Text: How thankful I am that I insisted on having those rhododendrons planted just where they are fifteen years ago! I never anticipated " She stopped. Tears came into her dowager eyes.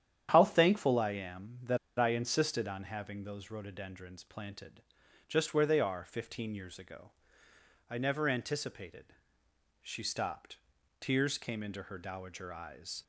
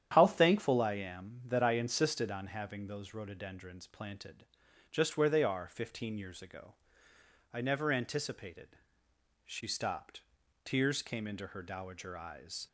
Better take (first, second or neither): second